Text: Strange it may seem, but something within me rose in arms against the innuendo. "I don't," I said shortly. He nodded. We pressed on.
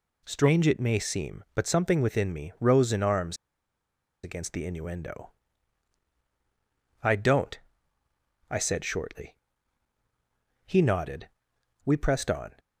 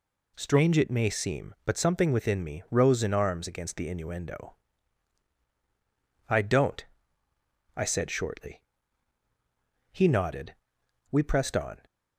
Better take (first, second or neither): second